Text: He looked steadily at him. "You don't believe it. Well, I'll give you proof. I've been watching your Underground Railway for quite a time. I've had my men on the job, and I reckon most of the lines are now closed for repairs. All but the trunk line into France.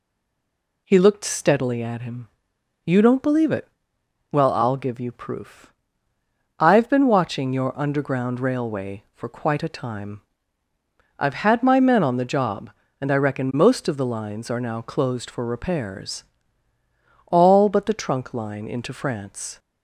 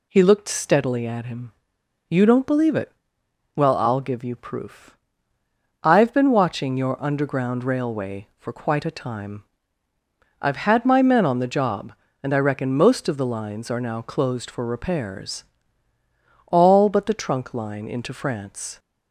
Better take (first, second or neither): second